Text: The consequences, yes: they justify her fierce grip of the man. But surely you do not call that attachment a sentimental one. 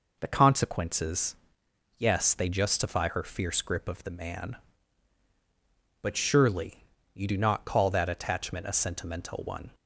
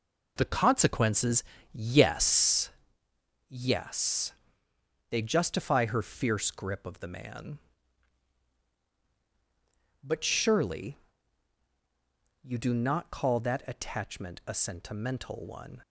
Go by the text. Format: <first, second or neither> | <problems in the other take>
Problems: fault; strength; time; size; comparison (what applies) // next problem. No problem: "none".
first | says "yes" twice; at 3.4 s // pauses between "surely" and "you"; strong; at 10.9 s; 1.4 s long; slight in the first